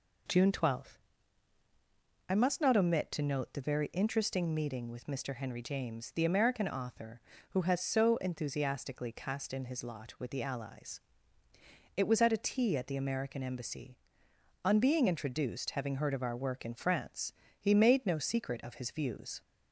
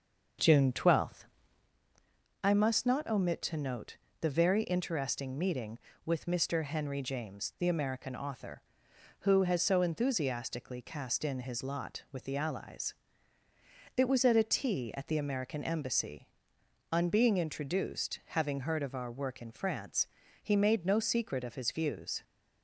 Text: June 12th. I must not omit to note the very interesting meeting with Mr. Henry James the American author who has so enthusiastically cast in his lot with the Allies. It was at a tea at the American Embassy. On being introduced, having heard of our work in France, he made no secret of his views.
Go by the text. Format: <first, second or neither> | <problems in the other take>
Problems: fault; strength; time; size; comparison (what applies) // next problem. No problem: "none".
first | starts louder than the rest; until 1.8 s; 6.5 dB // pauses between "note" and "the"; slight; at 3.9 s; 0.24 s long